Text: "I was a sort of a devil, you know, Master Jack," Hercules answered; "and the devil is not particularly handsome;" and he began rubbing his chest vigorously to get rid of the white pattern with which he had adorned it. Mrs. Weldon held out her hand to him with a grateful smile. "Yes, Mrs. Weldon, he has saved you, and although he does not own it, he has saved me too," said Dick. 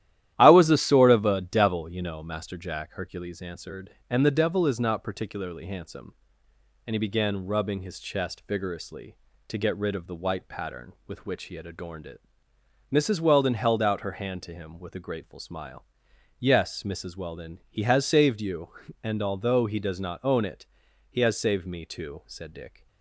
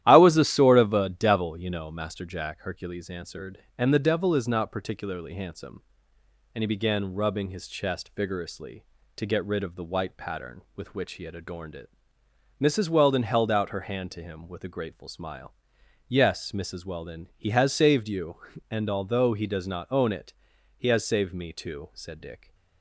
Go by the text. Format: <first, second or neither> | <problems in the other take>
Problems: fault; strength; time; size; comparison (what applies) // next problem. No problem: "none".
neither | starts louder than the rest; strong; the same in both